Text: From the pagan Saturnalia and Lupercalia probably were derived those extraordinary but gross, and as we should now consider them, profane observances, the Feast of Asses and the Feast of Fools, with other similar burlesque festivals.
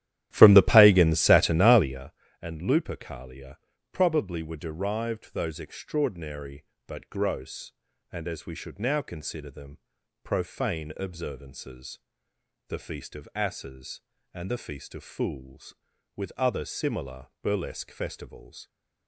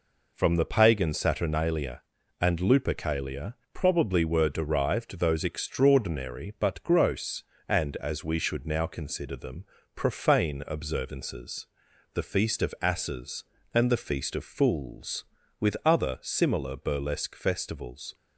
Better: second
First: starts louder than the rest; strong; until 2.1 s; 12.5 dB // pauses between "Lupercalia" and "probably"; slight; at 3.5 s; 0.34 s long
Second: pauses between "Lupercalia" and "probably"; slight; at 3.5 s; 0.18 s long

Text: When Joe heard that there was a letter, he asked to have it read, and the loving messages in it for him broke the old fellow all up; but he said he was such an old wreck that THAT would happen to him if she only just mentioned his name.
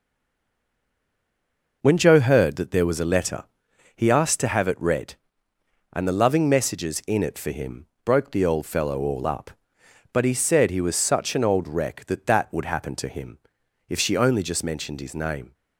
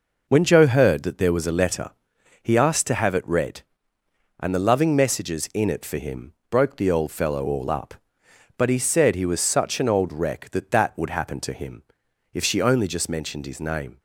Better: second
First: stays silent before the first word; noticeable; until 1.8 s; 1.8 s long // pauses between "him" and "broke"; slight; at 7.8 s; 0.18 s long // pauses between "him" and "if"; noticeable; at 13.3 s; 0.50 s long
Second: pauses between "him" and "broke"; slight; at 6.3 s; 0.16 s long // pauses between "him" and "if"; noticeable; at 11.8 s; 0.50 s long

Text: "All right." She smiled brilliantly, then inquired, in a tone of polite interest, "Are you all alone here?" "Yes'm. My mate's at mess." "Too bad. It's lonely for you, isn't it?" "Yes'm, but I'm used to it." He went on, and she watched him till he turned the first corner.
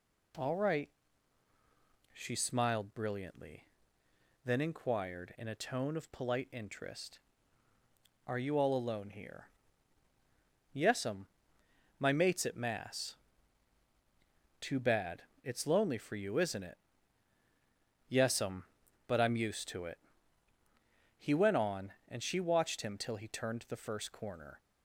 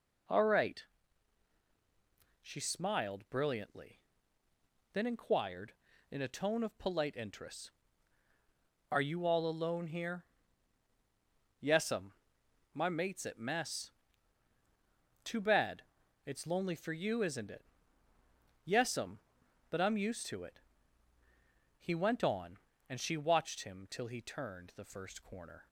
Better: second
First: says "mass" for "mess"; at 12.5 s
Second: none

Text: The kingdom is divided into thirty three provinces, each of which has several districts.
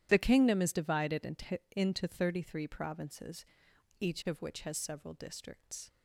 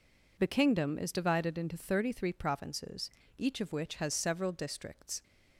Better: second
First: starts louder than the rest; strong; until 1.1 s; 11.5 dB // says "into" twice; at 1.7 s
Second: none

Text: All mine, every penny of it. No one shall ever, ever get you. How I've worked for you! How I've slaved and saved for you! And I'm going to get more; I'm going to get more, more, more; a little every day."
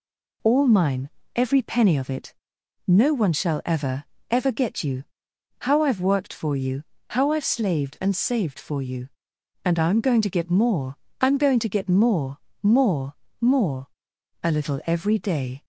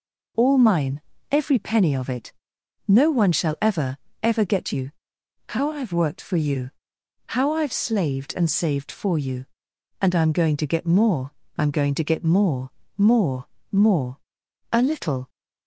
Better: first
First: none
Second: stops before "every day"; at 15.2 s

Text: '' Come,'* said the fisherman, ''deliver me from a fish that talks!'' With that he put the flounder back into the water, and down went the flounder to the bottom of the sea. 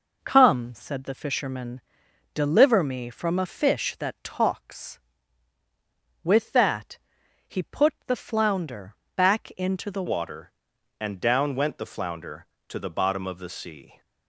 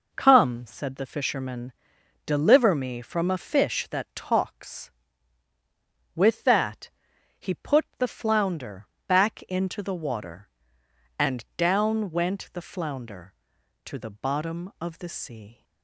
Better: second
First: pauses between "that" and "he"; noticeable; at 6.9 s; 0.50 s long // pauses between "flounder" and "back"; slight; at 8.9 s; 0.20 s long // changes voice at "water"; from 10.0 s on; 4.0 s long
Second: pauses between "that" and "he"; noticeable; at 6.9 s; 0.50 s long // pauses between "flounder" and "back"; slight; at 8.8 s; 0.20 s long

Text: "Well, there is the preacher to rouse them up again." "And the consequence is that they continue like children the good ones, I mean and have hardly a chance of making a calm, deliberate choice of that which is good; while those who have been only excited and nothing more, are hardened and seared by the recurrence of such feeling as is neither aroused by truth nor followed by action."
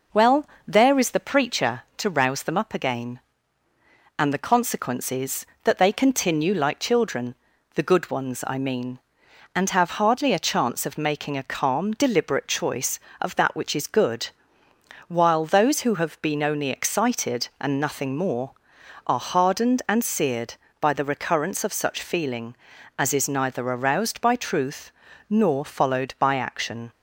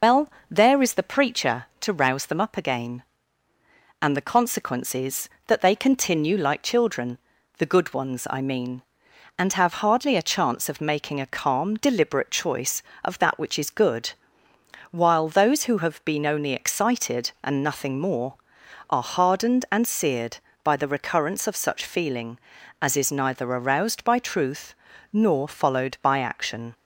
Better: first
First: pauses between "children" and "the"; at 7.3 s; 0.40 s long // pauses between "truth" and "nor"; at 24.9 s; 0.38 s long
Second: loses the start of "Well"; at 0.0 s; 75 ms // pauses between "children" and "the"; at 7.1 s; 0.40 s long // pauses between "truth" and "nor"; at 24.7 s; 0.38 s long

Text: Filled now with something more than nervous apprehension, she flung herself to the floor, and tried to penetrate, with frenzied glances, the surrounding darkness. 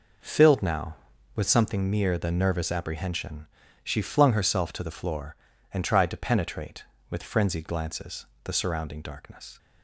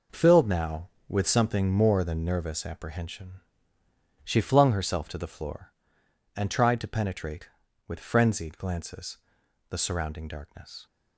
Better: second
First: says "mere" for "more"; at 1.8 s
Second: none

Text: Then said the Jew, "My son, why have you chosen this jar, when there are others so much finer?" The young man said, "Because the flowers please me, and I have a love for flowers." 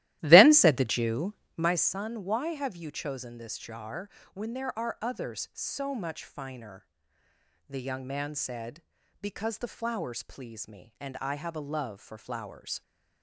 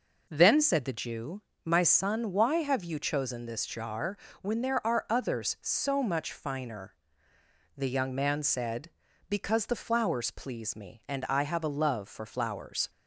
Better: second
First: starts louder than the rest; strong; until 1.8 s; 15 dB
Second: none

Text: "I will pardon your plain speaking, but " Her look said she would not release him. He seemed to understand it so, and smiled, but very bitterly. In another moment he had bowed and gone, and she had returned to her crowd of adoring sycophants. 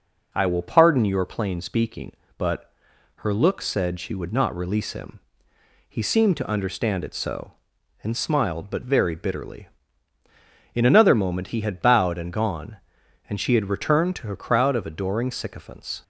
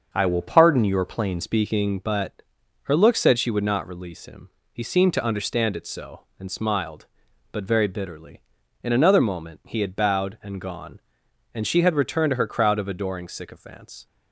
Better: first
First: none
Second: starts louder than the rest; until 1.1 s; 6.5 dB // changes voice at "speaking"; from 1.4 s on; 12.6 s long

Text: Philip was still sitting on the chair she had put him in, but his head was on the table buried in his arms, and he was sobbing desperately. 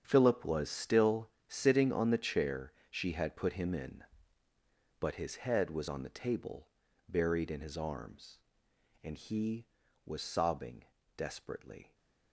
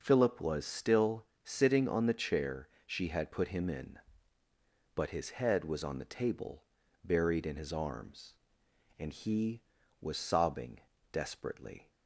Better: second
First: gets quieter; strong; throughout; 13 dB // pauses between "still" and "sitting"; slight; at 1.2 s; 0.18 s long // pauses between "chair" and "she"; slight; at 2.7 s; 0.20 s long // pauses between "table" and "buried"; at 6.6 s; 0.40 s long // pauses between "sobbing" and "desperately"; slight; at 10.8 s; 0.32 s long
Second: pauses between "still" and "sitting"; slight; at 1.2 s; 0.18 s long // pauses between "chair" and "she"; slight; at 2.6 s; 0.20 s long // pauses between "table" and "buried"; at 6.6 s; 0.40 s long // pauses between "sobbing" and "desperately"; slight; at 10.7 s; 0.32 s long

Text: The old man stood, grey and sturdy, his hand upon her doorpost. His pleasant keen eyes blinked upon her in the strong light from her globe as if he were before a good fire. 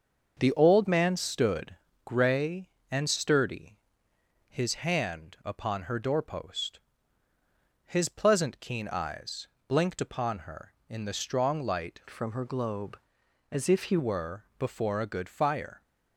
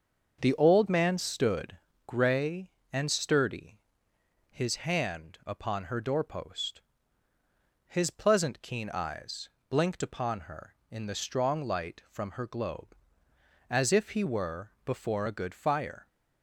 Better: second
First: starts louder than the rest; until 1.4 s; 6.5 dB // pauses between "eyes" and "blinked"; slight; at 9.4 s; 0.18 s long // changes voice from "from" to "he"; from 12.0 to 13.9 s; 1.9 s long // pauses between "were" and "before"; slight; at 14.4 s; 0.16 s long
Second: starts louder than the rest; until 1.4 s; 6.5 dB // pauses between "eyes" and "blinked"; slight; at 9.4 s; 0.18 s long // pauses between "were" and "before"; slight; at 14.7 s; 0.16 s long

